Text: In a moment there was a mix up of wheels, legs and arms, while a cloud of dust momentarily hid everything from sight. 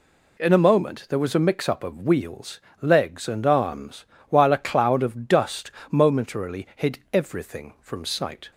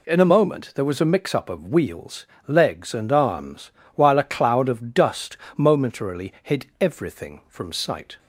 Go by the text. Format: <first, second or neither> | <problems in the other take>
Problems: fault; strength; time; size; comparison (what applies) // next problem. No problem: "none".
neither | pauses between "dust" and "momentarily"; slight; the same in both